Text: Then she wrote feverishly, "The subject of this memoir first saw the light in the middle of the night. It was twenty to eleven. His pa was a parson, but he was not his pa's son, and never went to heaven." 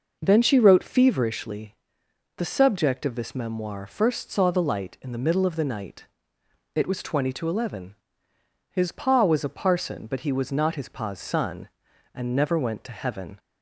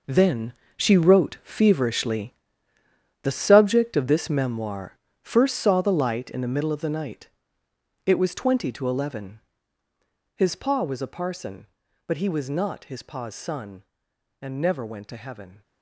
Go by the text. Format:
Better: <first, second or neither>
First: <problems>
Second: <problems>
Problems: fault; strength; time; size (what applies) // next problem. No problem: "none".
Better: first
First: none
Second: gets quieter; strong; throughout; 12 dB // pauses between "Then" and "she"; slight; at 0.5 s; 0.24 s long // pauses between "memoir" and "first"; slight; at 4.9 s; 0.24 s long